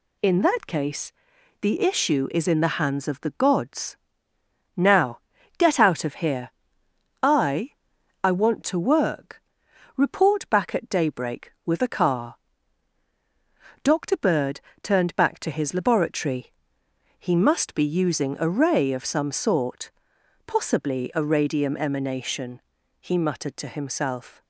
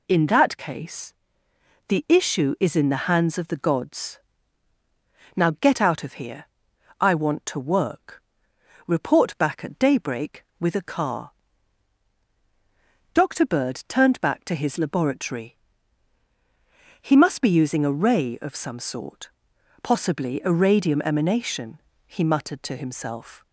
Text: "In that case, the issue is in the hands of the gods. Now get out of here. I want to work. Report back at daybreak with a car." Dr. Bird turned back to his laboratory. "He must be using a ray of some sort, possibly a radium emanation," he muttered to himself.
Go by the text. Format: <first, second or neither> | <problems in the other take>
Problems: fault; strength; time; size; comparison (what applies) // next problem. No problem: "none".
second | pauses between "Now" and "get"; at 5.2 s; 0.38 s long // says "I" twice; at 8.2 s // pauses between "Bird" and "turned"; slight; at 14.6 s; 0.22 s long